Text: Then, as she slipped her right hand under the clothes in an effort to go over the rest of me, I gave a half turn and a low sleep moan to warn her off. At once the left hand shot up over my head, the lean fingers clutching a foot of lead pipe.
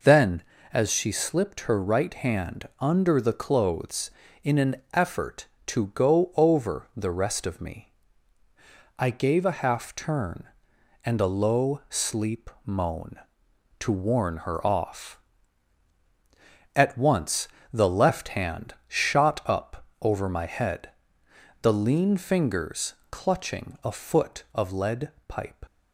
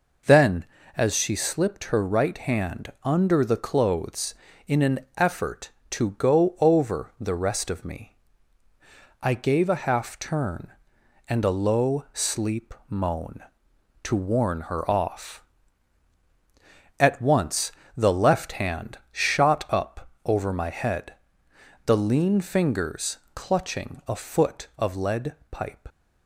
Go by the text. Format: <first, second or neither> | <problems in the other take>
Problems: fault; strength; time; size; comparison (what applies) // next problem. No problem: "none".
neither | pauses between "an" and "effort"; slight; the same in both // pauses between "sleep" and "moan"; slight; the same in both // pauses between "once" and "the"; slight; the same in both // pauses between "up" and "over"; slight; the same in both // pauses between "fingers" and "clutching"; slight; the same in both // pauses between "lead" and "pipe"; slight; the same in both